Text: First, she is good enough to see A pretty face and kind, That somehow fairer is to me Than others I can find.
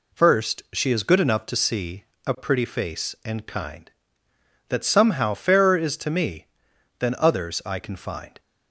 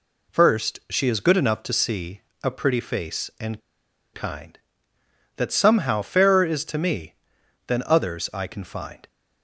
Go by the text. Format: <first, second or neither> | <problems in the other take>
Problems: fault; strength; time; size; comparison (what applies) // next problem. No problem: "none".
first | pauses between "see" and "A"; slight; at 2.1 s; 0.24 s long; slight in the first // pauses between "and" and "kind"; noticeable; at 3.5 s; 0.53 s long